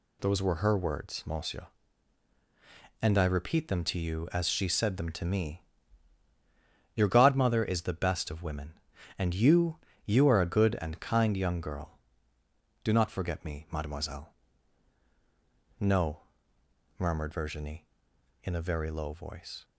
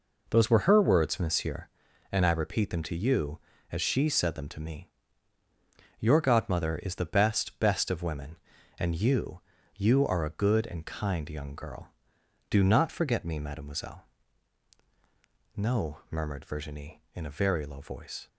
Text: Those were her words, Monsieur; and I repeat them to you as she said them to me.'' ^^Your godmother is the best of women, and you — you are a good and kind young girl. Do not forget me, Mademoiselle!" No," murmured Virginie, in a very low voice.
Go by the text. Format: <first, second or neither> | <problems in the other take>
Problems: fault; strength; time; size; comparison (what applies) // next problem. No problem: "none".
first | says "best" twice; at 7.5 s